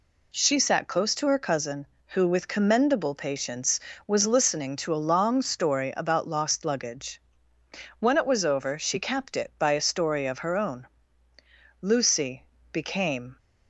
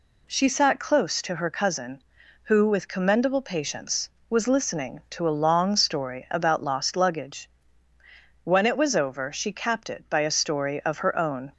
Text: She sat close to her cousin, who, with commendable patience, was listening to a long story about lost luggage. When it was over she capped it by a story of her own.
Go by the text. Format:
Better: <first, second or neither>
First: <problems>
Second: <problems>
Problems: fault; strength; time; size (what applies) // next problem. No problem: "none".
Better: second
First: goes on to say "Lucy became"; from 11.8 s on; 1.5 s long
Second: none